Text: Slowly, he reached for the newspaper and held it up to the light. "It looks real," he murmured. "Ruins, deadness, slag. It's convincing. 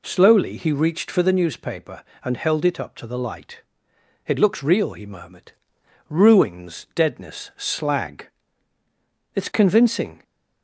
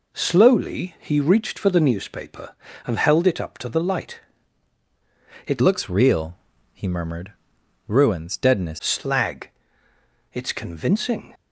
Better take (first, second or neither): first